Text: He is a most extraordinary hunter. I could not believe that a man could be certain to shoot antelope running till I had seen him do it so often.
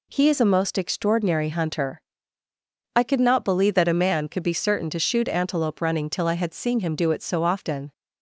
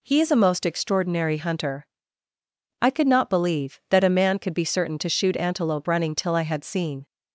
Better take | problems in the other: first | stops before "him do it so often"; at 7.0 s

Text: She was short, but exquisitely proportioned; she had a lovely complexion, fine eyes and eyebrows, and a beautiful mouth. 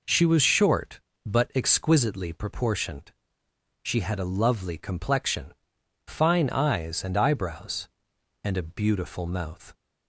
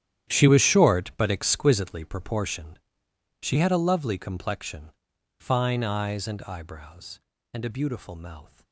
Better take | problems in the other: first | gets quieter; strong; throughout; 15.5 dB

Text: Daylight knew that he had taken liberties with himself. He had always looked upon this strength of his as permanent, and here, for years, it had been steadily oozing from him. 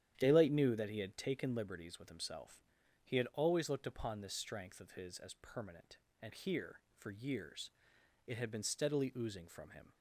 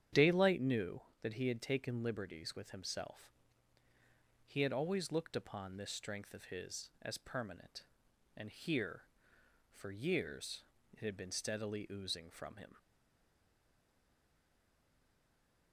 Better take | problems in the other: first | starts louder than the rest; strong; until 1.3 s; 9.5 dB; strong in the first // stays silent after the last word; strong; from 12.7 s on; 3.0 s long

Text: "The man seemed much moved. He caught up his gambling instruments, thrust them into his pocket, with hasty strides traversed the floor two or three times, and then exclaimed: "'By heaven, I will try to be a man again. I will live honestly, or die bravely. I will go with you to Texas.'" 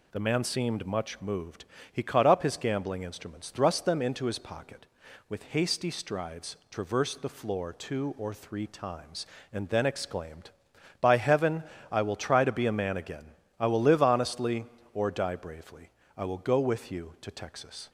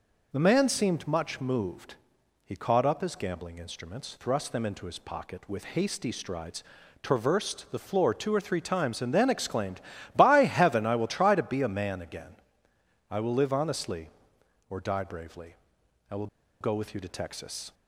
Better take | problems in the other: first | pauses between "strides" and "traversed"; at 6.6 s; 0.40 s long // pauses between "will" and "go"; slight; at 16.2 s; 0.34 s long

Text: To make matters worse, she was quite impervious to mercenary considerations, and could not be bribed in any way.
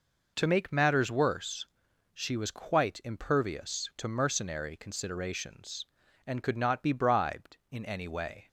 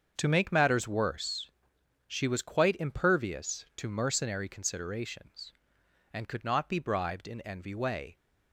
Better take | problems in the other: first | starts louder than the rest; until 1.1 s; 7 dB // says "envy" for "any"; at 7.4 s

